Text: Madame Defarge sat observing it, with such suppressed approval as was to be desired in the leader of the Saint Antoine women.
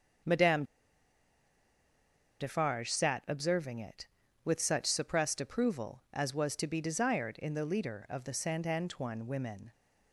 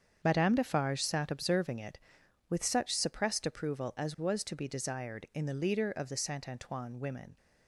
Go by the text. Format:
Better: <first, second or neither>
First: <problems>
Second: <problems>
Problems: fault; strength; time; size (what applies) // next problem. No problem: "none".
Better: second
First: starts louder than the rest; until 3.0 s; 7 dB // pauses between "Madame" and "Defarge"; strong; at 0.6 s; 1.7 s long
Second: starts louder than the rest; strong; until 1.2 s; 7 dB